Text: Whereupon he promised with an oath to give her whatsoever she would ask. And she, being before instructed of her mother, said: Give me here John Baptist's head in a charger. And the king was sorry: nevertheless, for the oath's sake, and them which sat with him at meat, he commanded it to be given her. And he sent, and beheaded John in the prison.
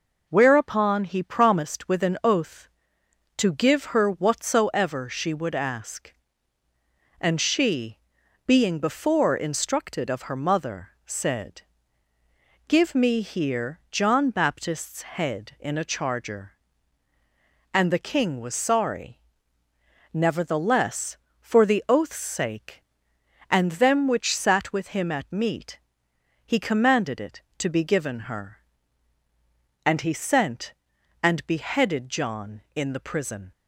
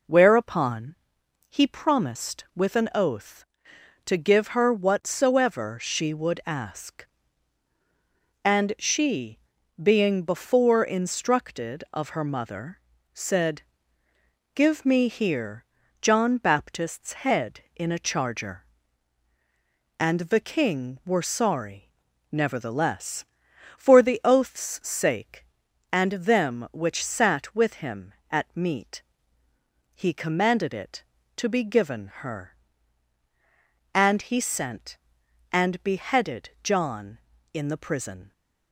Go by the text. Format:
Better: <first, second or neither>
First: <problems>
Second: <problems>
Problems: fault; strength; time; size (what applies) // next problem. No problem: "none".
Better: first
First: none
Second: pauses between "Whereupon" and "he"; noticeable; at 0.9 s; 0.54 s long // pauses between "here" and "John"; slight; at 15.6 s; 0.36 s long // says "were" for "was"; at 21.0 s